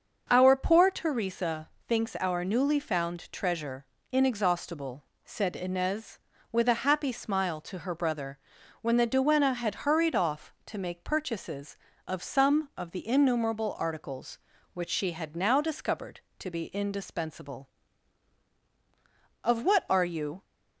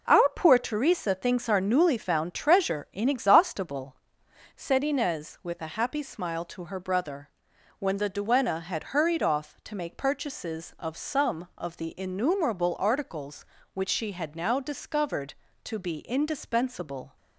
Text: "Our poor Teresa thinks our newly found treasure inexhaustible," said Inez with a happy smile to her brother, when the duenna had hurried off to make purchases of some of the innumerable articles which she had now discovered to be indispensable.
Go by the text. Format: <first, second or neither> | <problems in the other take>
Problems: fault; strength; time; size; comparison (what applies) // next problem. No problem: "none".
second | starts louder than the rest; until 1.3 s; 6.5 dB // pauses between "Teresa" and "thinks"; slight; at 1.6 s; 0.16 s long // pauses between "treasure" and "inexhaustible"; slight; at 3.8 s; 0.26 s long // goes on to say "Of what are you"; noticeable; from 19.4 s on; 1.0 s long